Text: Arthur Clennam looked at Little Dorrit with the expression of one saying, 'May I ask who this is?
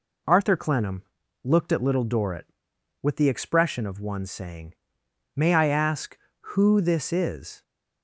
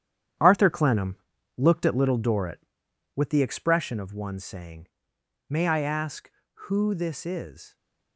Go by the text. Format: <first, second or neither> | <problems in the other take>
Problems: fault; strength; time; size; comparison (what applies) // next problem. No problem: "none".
first | gets quieter; strong; throughout; 9.5 dB // pauses between "Clennam" and "looked"; at 1.1 s; 0.40 s long; also in the first